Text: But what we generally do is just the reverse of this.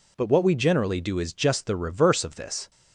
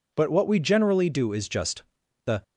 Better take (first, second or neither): first